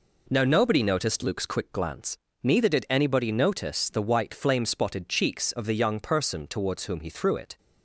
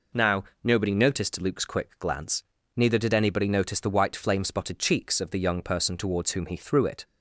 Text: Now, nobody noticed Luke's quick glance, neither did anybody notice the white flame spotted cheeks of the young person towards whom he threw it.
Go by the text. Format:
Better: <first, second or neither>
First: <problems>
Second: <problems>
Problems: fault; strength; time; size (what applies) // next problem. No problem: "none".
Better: neither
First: none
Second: none